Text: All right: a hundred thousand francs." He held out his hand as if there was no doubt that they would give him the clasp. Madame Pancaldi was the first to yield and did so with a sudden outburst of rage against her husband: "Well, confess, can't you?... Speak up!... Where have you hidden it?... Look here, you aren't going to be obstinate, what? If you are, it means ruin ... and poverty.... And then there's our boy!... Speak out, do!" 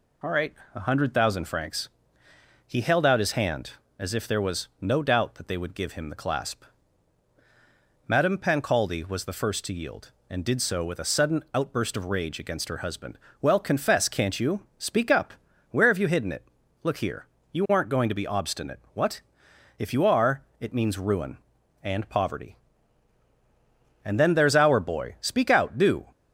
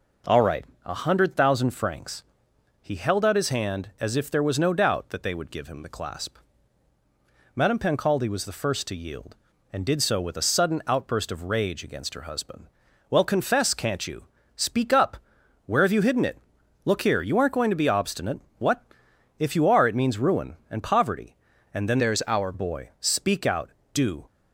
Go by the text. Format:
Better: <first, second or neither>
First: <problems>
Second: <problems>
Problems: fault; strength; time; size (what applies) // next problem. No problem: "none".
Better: first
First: none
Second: changes voice from "there's" to "our"; from 21.9 to 22.5 s; 0.6 s long